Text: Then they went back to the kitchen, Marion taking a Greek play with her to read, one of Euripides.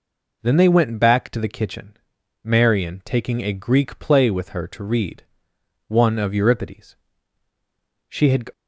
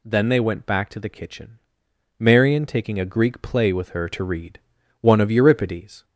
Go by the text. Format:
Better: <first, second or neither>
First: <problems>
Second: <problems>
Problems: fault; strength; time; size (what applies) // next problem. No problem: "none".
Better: second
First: goes on to say "She had"; slight; from 8.0 s on; 0.42 s long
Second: none